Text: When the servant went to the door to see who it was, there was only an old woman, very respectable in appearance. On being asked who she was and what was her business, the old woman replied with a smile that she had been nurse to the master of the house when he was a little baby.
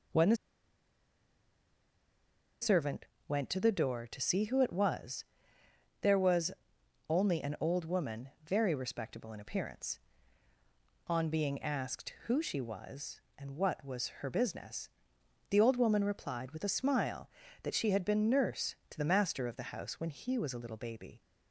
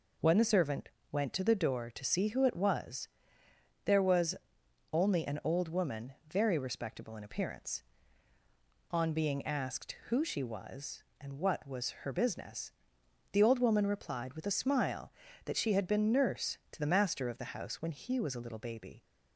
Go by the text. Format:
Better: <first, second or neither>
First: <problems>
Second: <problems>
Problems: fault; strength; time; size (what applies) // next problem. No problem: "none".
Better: second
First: pauses between "the" and "servant"; strong; at 0.3 s; 2.2 s long // pauses between "servant" and "went"; slight; at 3.0 s; 0.20 s long // pauses between "was" and "only"; noticeable; at 6.5 s; 0.58 s long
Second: pauses between "servant" and "went"; slight; at 0.9 s; 0.20 s long // pauses between "was" and "only"; noticeable; at 4.3 s; 0.58 s long